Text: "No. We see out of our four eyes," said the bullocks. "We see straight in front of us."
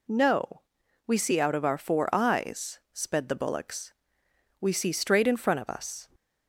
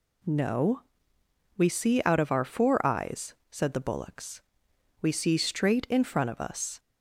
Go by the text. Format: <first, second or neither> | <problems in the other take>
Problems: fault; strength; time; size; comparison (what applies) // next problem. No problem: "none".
second | says "sped" for "said"; at 2.9 s